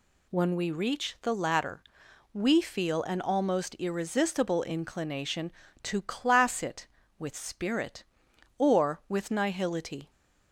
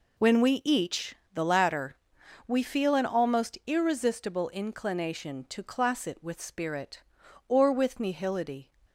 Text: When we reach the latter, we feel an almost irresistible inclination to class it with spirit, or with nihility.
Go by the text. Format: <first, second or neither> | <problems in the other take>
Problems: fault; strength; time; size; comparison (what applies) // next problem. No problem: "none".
first | says "each" for "reach"; at 0.6 s